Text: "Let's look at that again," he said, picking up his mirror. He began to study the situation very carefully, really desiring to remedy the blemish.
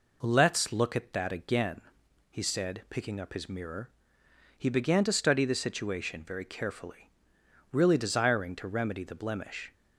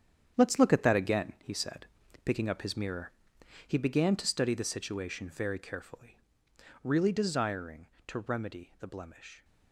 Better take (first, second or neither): first